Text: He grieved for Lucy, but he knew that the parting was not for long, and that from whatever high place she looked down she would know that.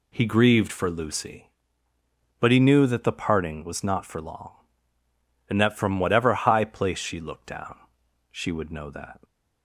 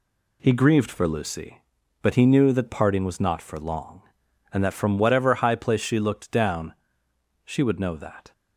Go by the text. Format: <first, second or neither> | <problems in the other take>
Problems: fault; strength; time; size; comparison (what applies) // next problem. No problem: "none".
first | skips "the"; at 2.6 s // pauses between "down" and "she"; noticeable; at 6.7 s; 0.72 s long; noticeable in the first